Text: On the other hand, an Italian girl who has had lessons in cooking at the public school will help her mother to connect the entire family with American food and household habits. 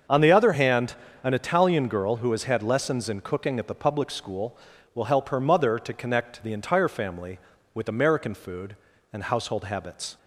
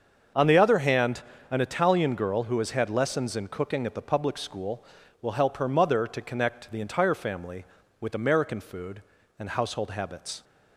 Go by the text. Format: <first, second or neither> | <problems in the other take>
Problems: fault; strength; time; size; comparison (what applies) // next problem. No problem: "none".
neither | starts louder than the rest; the same in both